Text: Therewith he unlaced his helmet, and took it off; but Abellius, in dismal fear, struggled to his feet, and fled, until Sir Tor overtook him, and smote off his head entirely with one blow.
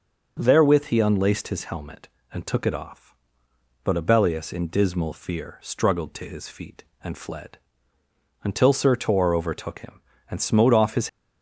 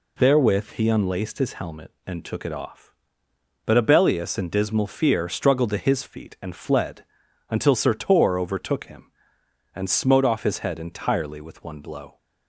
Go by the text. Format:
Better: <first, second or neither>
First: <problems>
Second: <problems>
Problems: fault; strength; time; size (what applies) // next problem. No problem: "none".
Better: second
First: stops before "head entirely with one blow"; at 11.0 s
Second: none